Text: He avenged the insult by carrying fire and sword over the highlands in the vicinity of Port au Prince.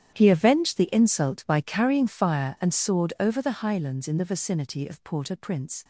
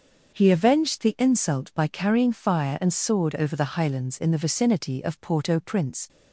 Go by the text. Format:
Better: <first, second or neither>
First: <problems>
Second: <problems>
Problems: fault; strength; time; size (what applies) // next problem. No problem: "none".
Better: second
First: gets quieter; strong; throughout; 16.5 dB // starts louder than the rest; strong; until 1.1 s; 10.5 dB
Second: starts louder than the rest; until 1.3 s; 6.5 dB